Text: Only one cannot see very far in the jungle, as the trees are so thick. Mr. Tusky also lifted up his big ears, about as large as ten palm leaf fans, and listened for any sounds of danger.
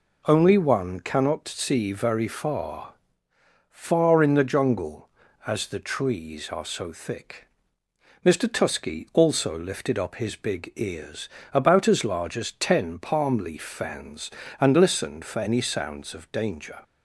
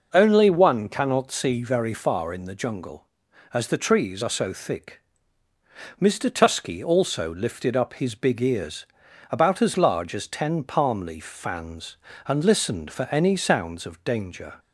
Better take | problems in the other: second | says "far" twice; at 3.6 s

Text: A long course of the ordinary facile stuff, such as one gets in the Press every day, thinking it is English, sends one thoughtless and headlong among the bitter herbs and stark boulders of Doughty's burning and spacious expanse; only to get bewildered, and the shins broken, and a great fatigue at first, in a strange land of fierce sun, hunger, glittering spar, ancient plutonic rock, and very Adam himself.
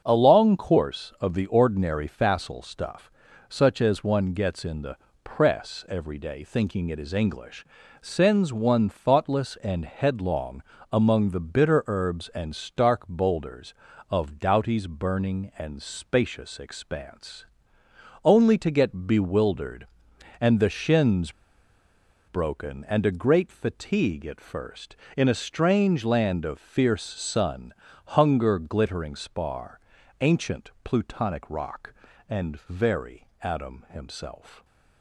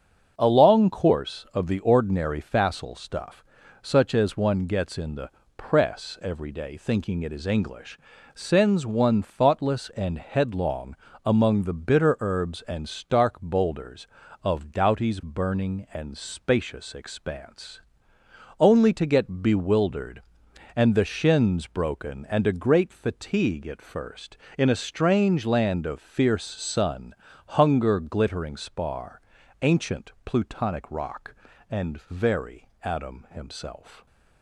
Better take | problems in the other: second | starts louder than the rest; until 1.0 s; 6.5 dB; also in the second // pauses between "the" and "Press"; slight; at 4.9 s; 0.28 s long; slight in the second // pauses between "headlong" and "among"; slight; at 10.6 s; 0.28 s long; slight in the second // pauses between "shins" and "broken"; noticeable; at 21.3 s; 0.97 s long

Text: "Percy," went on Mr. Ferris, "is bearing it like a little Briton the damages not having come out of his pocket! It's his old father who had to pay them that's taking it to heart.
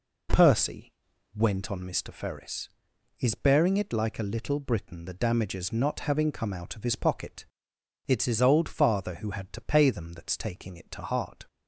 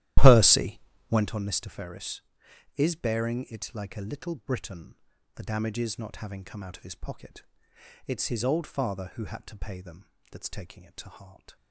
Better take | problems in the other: first | starts louder than the rest; strong; until 1.4 s; 14 dB // pauses between "Briton" and "the"; at 4.9 s; 0.40 s long // pauses between "them" and "that's"; slight; at 10.0 s; 0.22 s long

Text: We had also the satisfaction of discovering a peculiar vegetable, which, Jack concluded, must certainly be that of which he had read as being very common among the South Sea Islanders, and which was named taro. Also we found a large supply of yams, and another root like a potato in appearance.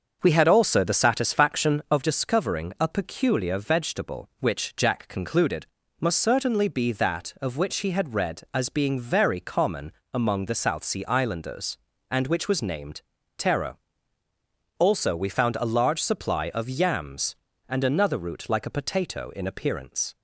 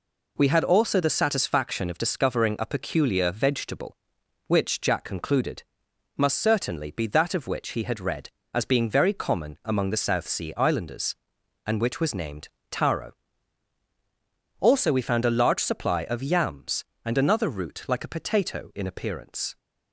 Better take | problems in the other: second | starts louder than the rest; until 2.0 s; 6.5 dB // pauses between "common" and "among"; slight; at 9.9 s; 0.22 s long // pauses between "named" and "taro"; slight; at 13.0 s; 0.36 s long; slight in the second

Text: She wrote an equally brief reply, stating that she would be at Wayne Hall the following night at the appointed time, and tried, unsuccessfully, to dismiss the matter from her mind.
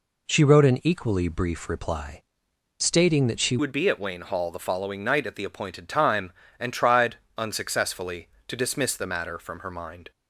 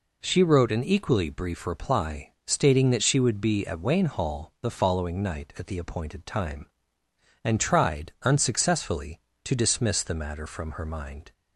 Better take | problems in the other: second | changes voice at "would"; from 3.5 s on; 6.6 s long

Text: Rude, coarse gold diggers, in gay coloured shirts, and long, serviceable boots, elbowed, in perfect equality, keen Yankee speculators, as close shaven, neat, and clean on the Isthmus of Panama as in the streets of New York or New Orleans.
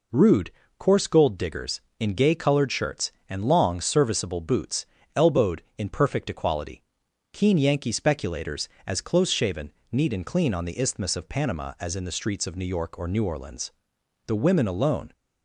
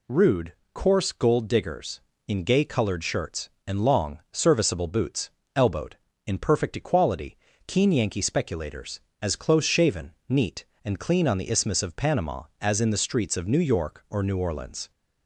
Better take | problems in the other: second | goes on to say "The women alone"; noticeable; from 14.2 s on; 0.86 s long

